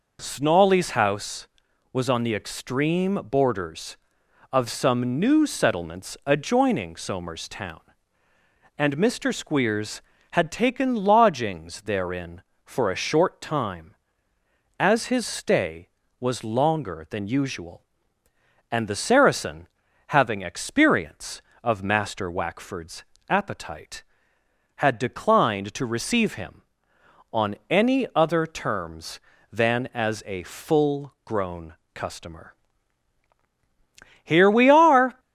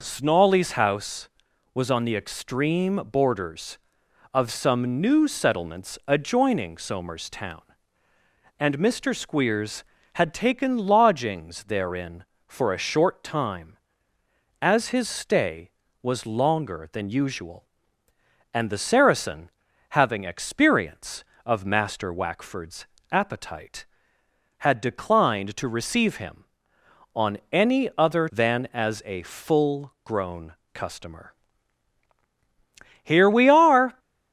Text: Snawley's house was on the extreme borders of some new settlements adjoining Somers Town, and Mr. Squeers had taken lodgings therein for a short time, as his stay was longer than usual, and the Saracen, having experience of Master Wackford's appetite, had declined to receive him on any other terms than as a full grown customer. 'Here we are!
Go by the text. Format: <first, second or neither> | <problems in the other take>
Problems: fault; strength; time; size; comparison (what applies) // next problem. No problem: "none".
first | pauses between "Wackford's" and "appetite"; slight; at 22.8 s; 0.26 s long; slight in the first // skips "terms"; at 28.2 s // pauses between "grown" and "customer"; slight; at 30.5 s; 0.18 s long; slight in the first